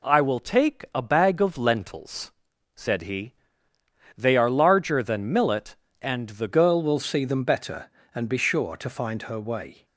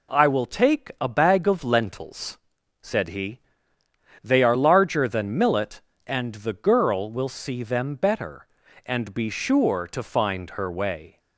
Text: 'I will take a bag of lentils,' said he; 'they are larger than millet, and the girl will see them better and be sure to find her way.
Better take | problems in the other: second | changes voice at "girl"; from 6.4 s on; 3.4 s long

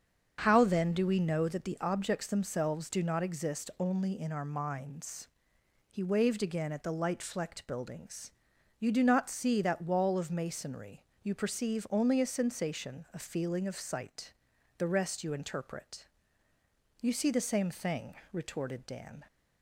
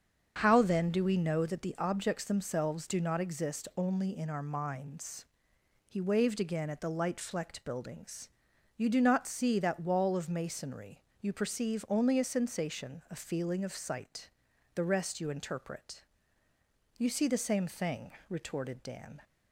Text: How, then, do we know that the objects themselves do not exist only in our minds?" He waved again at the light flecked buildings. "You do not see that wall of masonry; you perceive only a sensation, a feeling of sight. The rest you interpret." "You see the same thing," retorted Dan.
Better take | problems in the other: neither | starts louder than the rest; the same in both

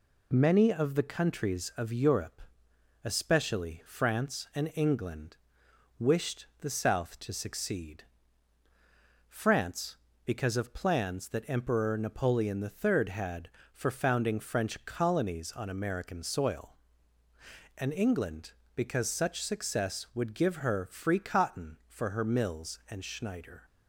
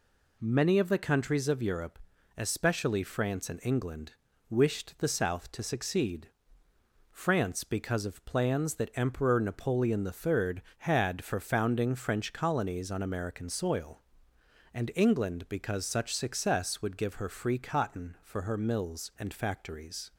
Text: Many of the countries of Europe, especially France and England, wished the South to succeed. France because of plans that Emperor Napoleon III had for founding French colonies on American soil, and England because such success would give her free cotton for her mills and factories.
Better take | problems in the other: second | pauses between "wished" and "the"; slight; at 6.4 s; 0.16 s long // says "schneider" for "factories"; at 23.0 s

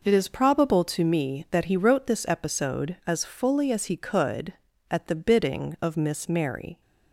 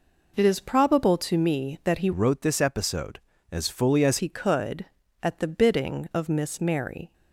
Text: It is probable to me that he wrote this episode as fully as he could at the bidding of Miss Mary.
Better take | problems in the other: first | changes voice from "wrote" to "as"; from 2.1 to 4.1 s; 2.0 s long

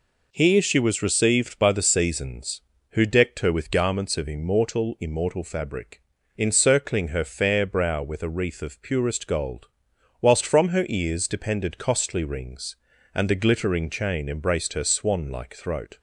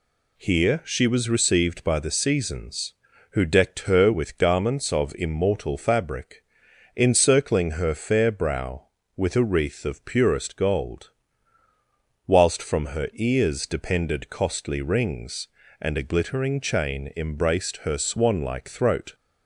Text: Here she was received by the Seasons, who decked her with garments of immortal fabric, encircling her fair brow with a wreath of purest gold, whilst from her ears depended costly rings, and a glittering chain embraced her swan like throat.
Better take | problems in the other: second | says "immortal" twice; at 4.9 s

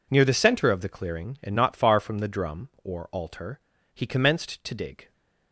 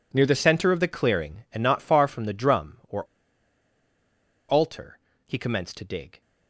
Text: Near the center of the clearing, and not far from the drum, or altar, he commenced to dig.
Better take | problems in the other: first | pauses between "or" and "altar"; strong; at 3.0 s; 1.4 s long

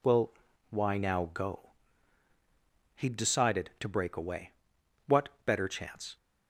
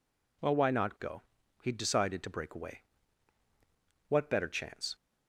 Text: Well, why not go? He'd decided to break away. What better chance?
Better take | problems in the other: second | says "now" for "not"; at 0.9 s

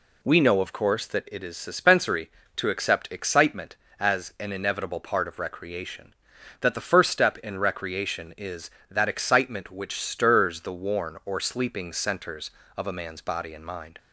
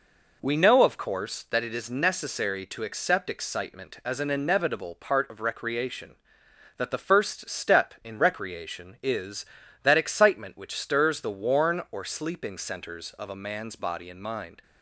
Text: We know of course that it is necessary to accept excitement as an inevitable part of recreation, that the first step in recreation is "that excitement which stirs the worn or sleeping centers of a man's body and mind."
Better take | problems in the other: second | says "suspensory" for "necessary"; at 1.5 s

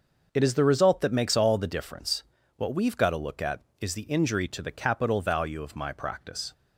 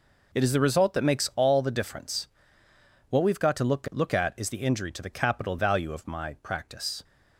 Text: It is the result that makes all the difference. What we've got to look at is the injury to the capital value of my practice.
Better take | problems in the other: first | says "look" twice; at 3.9 s

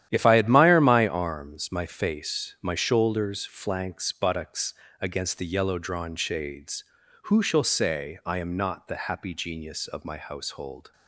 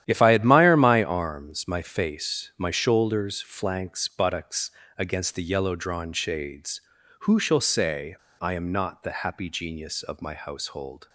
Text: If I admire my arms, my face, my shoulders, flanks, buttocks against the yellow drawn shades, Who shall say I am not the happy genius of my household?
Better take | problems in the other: first | starts louder than the rest; strong; until 1.0 s; 11 dB; strong in the first // pauses between "buttocks" and "against"; slight; at 4.7 s; 0.28 s long; slight in the first // pauses between "say" and "I"; slight; at 8.1 s; 0.24 s long

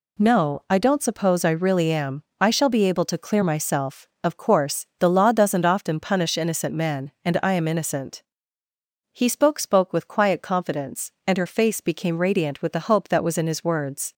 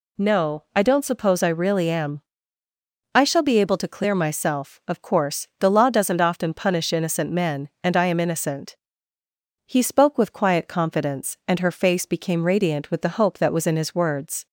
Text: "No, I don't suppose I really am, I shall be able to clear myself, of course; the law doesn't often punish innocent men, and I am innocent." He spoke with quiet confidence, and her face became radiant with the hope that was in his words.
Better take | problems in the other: second | says "spoke" twice; at 9.5 s

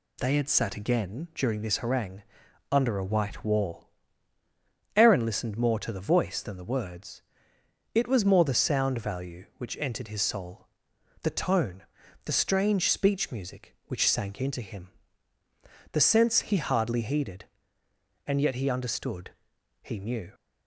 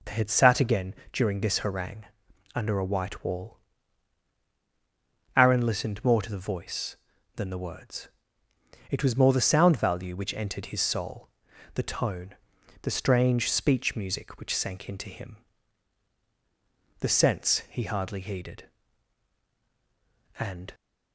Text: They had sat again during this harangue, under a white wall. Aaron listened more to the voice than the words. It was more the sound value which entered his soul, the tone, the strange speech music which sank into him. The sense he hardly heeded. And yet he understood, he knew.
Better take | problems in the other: first | pauses between "again" and "during"; slight; at 0.9 s; 0.18 s long // stops before "yet he understood he knew"; at 20.7 s

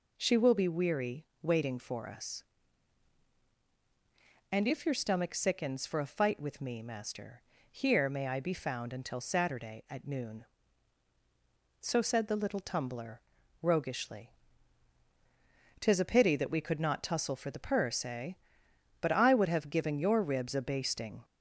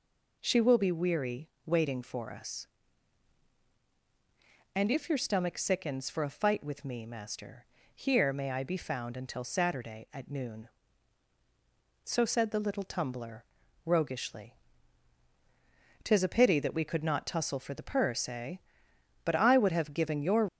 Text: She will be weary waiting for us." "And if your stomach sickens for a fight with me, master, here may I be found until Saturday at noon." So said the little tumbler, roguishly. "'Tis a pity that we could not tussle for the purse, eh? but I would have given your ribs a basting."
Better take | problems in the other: first | pauses between "weary" and "waiting"; slight; at 1.4 s; 0.16 s long; slight in the first // stops before "ribs a basting"; at 20.4 s

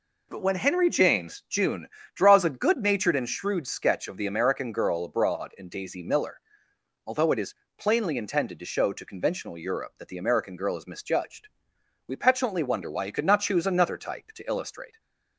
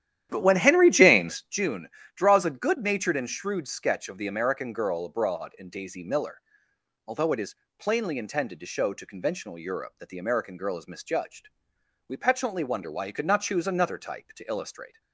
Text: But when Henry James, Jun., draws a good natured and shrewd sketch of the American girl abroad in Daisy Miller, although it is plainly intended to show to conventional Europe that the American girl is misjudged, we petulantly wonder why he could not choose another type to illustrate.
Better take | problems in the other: first | starts louder than the rest; strong; until 1.5 s; 11.5 dB // pauses between "is" and "plainly"; slight; at 7.5 s; 0.22 s long; slight in the first

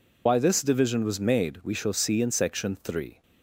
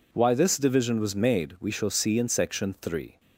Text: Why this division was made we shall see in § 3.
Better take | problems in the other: second | loses the start of "Why"; at 0.2 s; 80 ms

